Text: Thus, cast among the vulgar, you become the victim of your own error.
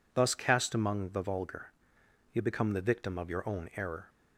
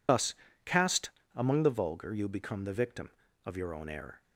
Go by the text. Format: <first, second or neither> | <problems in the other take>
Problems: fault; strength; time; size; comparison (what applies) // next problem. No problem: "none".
first | loses the start of "Thus"; at 0.0 s; 55 ms // pauses between "cast" and "among"; slight; at 1.0 s; 0.26 s long